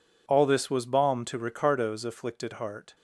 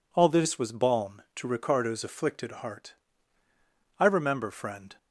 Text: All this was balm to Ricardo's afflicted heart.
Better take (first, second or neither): first